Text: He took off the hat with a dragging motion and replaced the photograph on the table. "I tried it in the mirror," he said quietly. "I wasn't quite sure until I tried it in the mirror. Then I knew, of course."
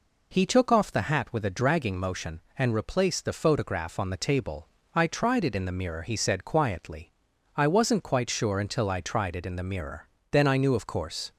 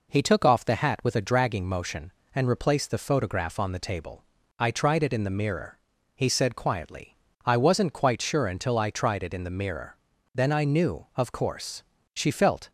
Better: first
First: none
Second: goes on to say "She felt"; from 12.1 s on; 0.58 s long

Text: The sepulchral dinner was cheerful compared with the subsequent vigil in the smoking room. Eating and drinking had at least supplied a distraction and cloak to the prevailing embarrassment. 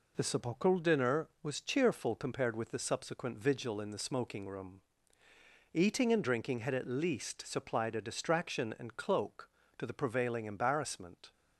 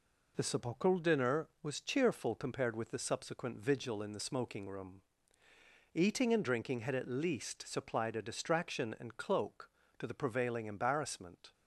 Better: neither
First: none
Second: none

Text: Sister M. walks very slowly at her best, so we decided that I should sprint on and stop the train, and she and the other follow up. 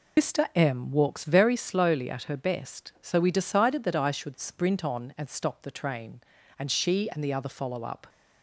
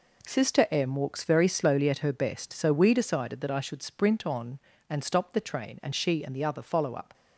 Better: second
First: loses the start of "Sister"; at 0.1 s; 160 ms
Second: none

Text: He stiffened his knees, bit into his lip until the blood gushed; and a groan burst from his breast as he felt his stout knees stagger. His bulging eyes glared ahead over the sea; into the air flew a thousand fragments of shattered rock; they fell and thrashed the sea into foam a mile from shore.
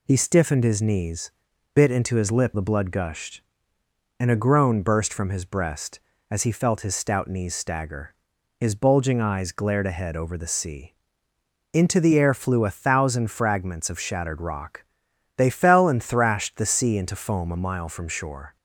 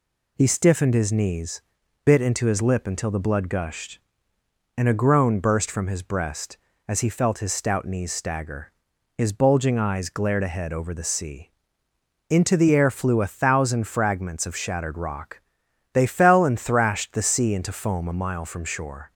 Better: second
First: skips "until"; at 2.5 s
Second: none

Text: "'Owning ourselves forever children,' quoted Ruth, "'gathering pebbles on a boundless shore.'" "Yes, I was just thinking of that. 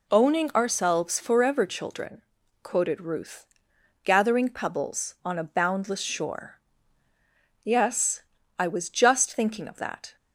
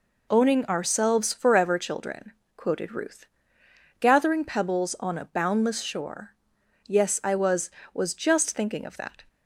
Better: first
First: none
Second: says "was" twice; at 7.9 s

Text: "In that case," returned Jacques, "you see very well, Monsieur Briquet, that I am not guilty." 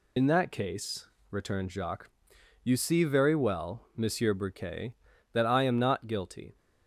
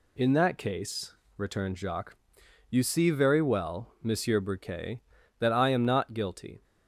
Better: second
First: loses the start of "In"; at 0.1 s; 65 ms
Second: none

